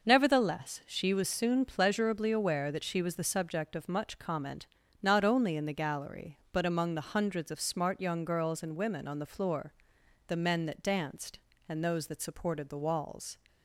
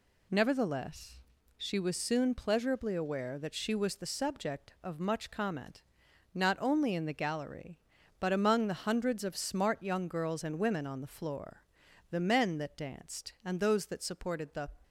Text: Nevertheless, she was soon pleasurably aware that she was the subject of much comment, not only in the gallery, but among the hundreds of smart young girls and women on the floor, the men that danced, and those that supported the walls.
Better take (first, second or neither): first